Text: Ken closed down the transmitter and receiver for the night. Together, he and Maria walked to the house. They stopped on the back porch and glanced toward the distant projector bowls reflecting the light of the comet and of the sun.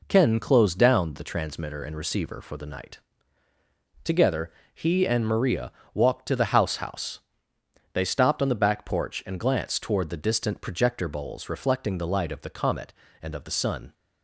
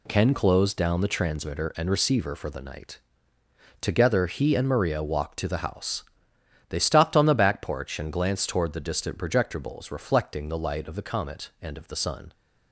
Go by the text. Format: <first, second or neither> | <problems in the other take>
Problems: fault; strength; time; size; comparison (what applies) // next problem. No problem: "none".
second | pauses between "Maria" and "walked"; slight; at 5.7 s; 0.22 s long // says "house" twice; at 6.7 s